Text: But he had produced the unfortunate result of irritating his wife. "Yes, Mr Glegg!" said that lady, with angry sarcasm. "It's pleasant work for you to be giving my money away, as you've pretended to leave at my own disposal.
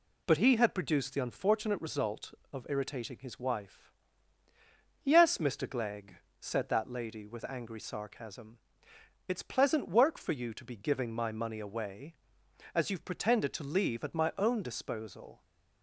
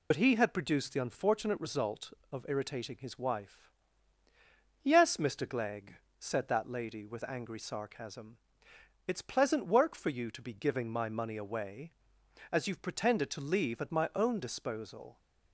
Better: first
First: none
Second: loses the start of "But"; at 0.1 s; 55 ms

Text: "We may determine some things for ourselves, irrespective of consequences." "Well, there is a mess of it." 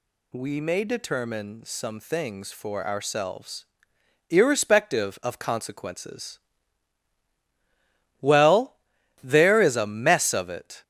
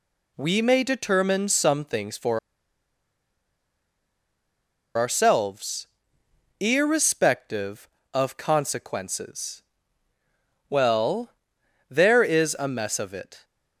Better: first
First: none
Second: pauses between "for" and "ourselves"; strong; at 2.3 s; 2.5 s long

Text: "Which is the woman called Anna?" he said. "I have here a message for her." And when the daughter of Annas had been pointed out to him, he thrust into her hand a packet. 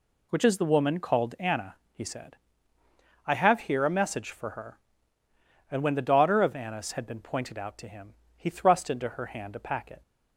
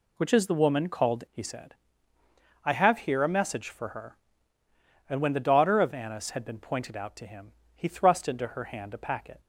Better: first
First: none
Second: skips "Anna"; at 1.2 s

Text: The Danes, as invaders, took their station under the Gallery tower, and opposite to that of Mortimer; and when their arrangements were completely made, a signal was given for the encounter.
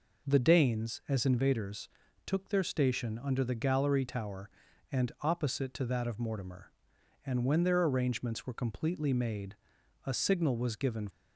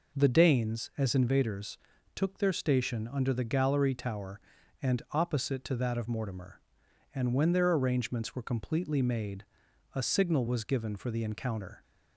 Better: second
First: stops before "for the encounter"; at 11.0 s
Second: none

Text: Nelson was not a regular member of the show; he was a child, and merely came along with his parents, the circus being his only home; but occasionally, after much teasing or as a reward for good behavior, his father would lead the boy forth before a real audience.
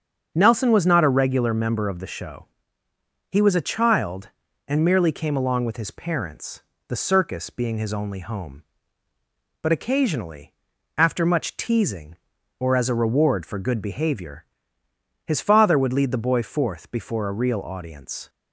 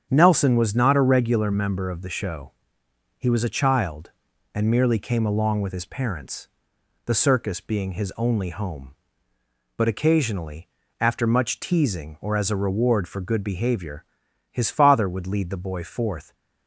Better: first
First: starts louder than the rest; strong; until 1.3 s; 7 dB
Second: starts louder than the rest; strong; until 1.1 s; 8.5 dB // stops before "before a real audience"; at 16.3 s

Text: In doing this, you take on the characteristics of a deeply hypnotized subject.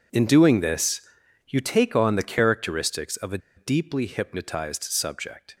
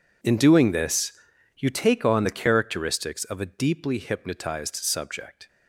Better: second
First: pauses between "a" and "deeply"; slight; at 3.3 s; 0.18 s long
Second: none

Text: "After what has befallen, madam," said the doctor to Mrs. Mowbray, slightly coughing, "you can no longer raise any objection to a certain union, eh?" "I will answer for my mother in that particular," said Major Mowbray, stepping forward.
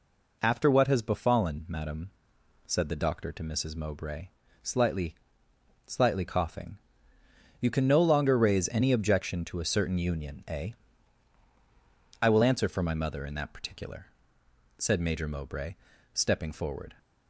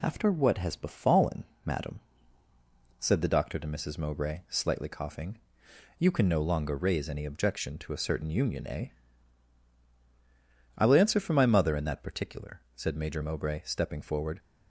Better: second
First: says "slightly" twice; at 5.8 s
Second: none

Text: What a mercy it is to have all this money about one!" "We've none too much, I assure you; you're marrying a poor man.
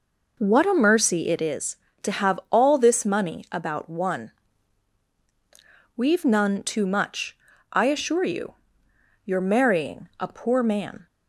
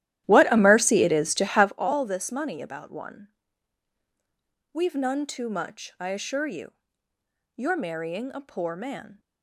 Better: first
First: none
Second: starts louder than the rest; strong; until 1.8 s; 13 dB

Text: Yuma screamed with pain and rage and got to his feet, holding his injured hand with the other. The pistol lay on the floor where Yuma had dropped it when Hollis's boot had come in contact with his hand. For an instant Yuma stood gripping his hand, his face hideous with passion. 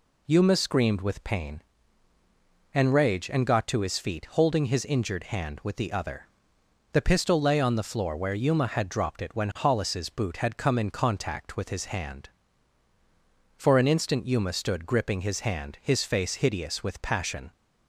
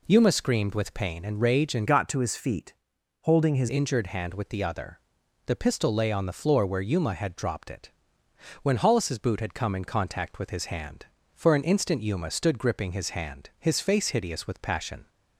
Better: first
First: none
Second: changes voice from "got" to "his"; from 1.8 to 3.6 s; 1.8 s long // pauses between "it" and "when"; noticeable; at 7.9 s; 0.72 s long

